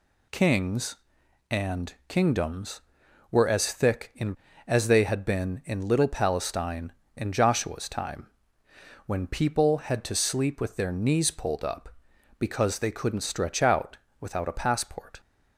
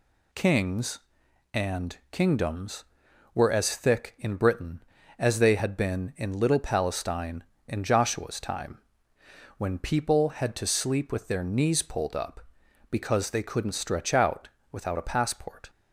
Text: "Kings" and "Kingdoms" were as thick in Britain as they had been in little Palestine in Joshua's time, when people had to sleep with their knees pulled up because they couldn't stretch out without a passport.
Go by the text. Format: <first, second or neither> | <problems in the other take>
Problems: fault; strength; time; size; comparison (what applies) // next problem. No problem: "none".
second | skips "Britain"; at 4.4 s // pauses between "out" and "without"; slight; at 13.9 s; 0.24 s long; slight in the second